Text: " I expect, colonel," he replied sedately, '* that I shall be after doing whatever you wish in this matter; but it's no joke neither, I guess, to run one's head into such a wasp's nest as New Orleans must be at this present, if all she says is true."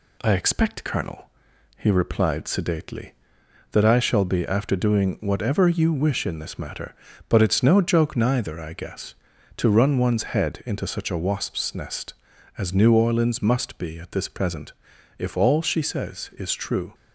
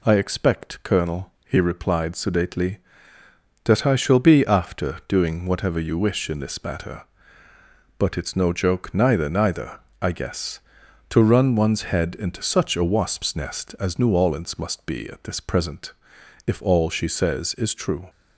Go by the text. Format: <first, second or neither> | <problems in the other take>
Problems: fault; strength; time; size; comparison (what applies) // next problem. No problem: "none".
first | says "neither" twice; at 9.2 s